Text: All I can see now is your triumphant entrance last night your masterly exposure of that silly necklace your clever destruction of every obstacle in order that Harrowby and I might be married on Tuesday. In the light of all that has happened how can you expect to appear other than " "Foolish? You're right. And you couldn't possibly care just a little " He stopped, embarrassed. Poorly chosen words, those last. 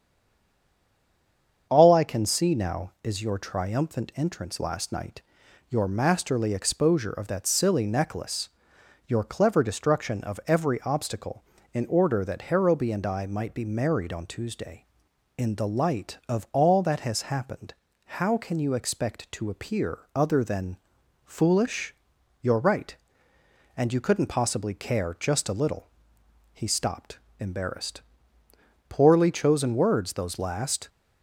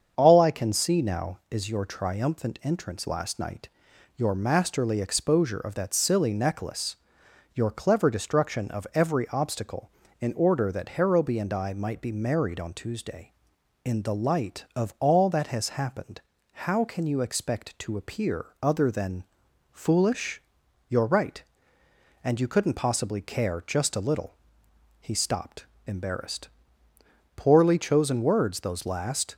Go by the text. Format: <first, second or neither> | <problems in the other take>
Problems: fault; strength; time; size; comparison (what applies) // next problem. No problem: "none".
second | stays silent before the first word; noticeable; until 1.7 s; 1.7 s long // starts louder than the rest; strong; until 2.7 s; 7 dB; strong in the second // pauses between "night" and "your"; noticeable; at 5.2 s; 0.48 s long; noticeable in the second // pauses between "necklace" and "your"; noticeable; at 8.4 s; 0.58 s long; noticeable in the second // pauses between "happened" and "how"; at 17.7 s; 0.42 s long; also in the second // pauses between "appear" and "other"; slight; at 19.9 s; 0.18 s long; slight in the second